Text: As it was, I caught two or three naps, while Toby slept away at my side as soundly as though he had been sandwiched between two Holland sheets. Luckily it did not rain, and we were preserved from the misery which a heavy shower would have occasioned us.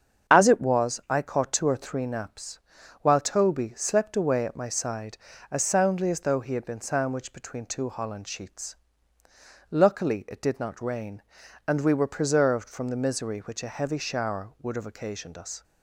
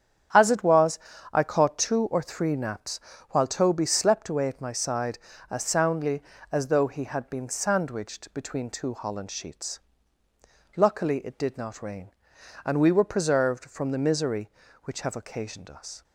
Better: first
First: starts louder than the rest; strong; until 1.3 s; 7.5 dB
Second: starts louder than the rest; strong; until 1.7 s; 9 dB // skips "a heavy shower would"; at 15.0 s

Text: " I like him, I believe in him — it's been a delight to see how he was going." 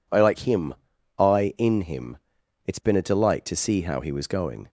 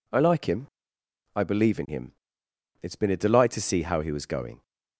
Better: second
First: skips "believe"; at 1.5 s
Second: none

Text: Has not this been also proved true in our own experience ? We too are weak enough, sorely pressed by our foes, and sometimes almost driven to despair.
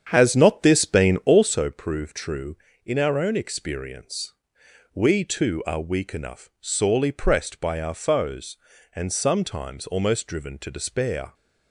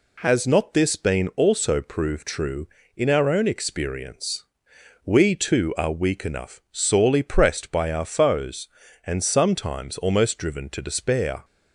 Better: second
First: starts louder than the rest; strong; until 1.6 s; 8 dB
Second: none

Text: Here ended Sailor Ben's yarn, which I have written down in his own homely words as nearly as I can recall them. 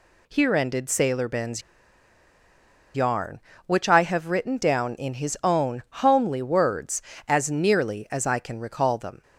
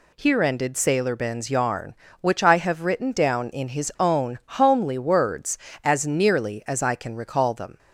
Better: second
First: pauses between "Ben's" and "yarn"; strong; at 1.6 s; 1.3 s long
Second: none

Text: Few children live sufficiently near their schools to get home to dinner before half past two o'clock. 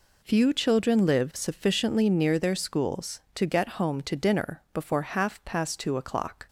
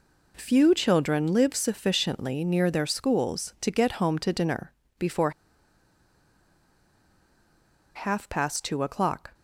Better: first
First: none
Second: pauses between "dinner" and "before"; slight; at 4.7 s; 0.26 s long // pauses between "before" and "half"; strong; at 5.2 s; 2.6 s long

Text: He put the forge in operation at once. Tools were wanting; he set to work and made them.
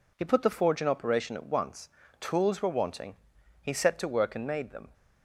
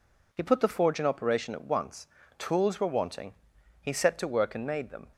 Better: neither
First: none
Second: none

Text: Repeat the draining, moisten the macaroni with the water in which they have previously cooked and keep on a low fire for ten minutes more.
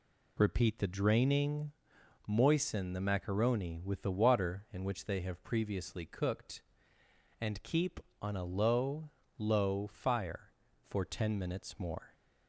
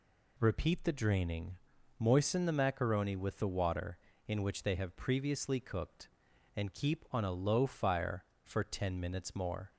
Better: second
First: says "low" twice; at 9.3 s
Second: none

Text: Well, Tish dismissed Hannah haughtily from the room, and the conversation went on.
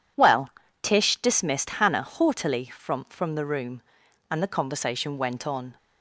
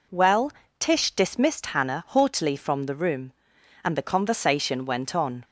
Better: second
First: says "from" twice; at 3.0 s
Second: none

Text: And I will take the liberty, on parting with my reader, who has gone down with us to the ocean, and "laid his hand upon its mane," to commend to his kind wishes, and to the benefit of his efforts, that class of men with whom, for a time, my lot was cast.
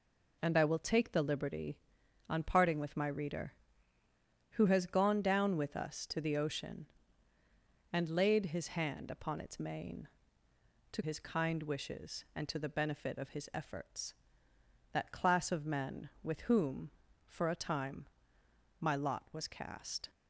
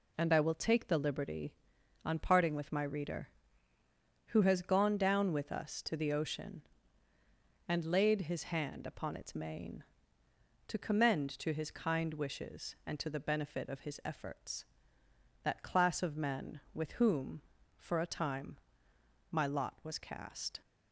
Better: second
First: skips "commend to"; at 11.0 s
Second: none

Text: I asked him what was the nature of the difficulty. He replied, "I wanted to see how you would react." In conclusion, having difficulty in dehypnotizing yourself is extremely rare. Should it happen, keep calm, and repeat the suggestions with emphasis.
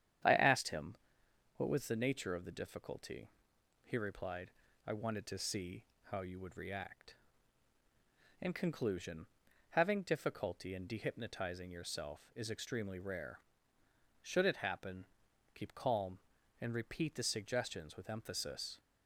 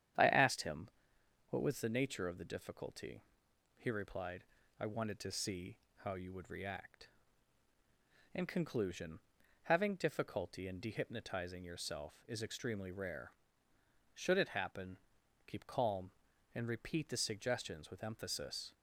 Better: neither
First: starts louder than the rest; strong; until 1.8 s; 9.5 dB // pauses between "him" and "what"; noticeable; at 0.9 s; 0.62 s long // pauses between "see" and "how"; slight; at 5.8 s; 0.20 s long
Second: starts louder than the rest; strong; until 1.8 s; 9.5 dB // pauses between "him" and "what"; noticeable; at 0.8 s; 0.62 s long // pauses between "see" and "how"; slight; at 5.7 s; 0.20 s long

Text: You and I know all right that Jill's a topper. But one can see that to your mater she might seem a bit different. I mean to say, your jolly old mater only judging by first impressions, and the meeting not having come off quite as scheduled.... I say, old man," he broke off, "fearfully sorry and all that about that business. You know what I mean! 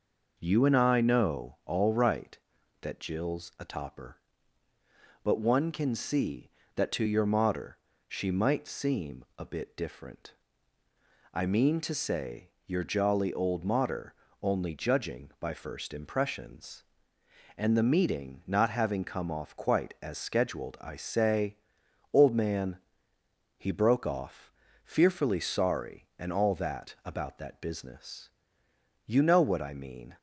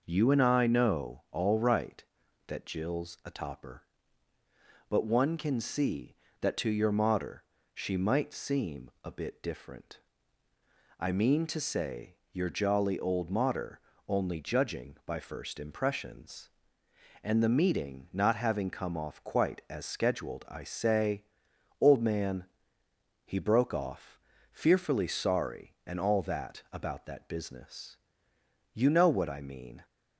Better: neither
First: pauses between "mater" and "she"; slight; at 7.7 s; 0.28 s long // pauses between "mater" and "only"; slight; at 14.1 s; 0.30 s long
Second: pauses between "mater" and "she"; slight; at 7.4 s; 0.28 s long // pauses between "mater" and "only"; slight; at 13.7 s; 0.30 s long

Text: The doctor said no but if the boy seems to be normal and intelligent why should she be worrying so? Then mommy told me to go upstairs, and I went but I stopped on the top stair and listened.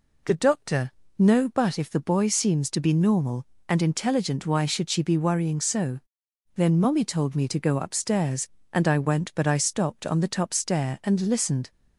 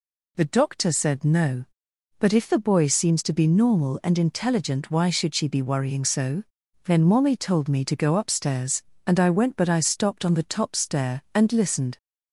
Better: second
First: skips "said"; at 1.0 s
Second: none

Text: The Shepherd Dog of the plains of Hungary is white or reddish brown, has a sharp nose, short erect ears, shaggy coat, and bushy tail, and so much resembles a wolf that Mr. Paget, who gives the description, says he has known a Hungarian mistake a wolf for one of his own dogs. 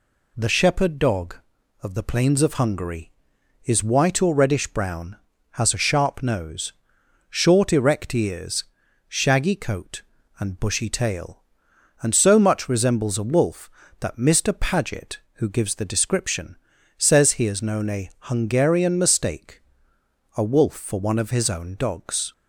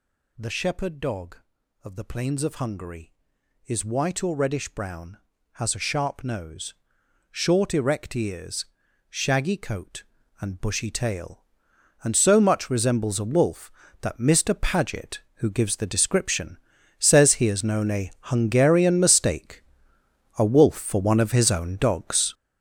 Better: first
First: pauses between "mistake" and "a"; noticeable; at 19.6 s; 0.76 s long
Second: gets louder; strong; throughout; 9.5 dB // pauses between "mistake" and "a"; noticeable; at 19.6 s; 0.76 s long

